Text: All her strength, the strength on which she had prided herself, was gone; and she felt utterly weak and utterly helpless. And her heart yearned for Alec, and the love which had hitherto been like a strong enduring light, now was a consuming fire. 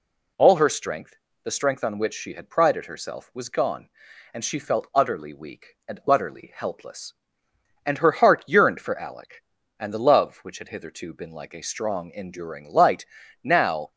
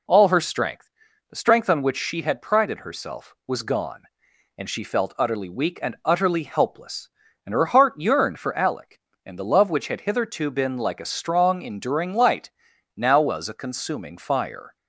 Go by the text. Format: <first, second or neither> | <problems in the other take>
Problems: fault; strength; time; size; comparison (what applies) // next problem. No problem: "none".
second | stops before "was a consuming fire"; at 13.9 s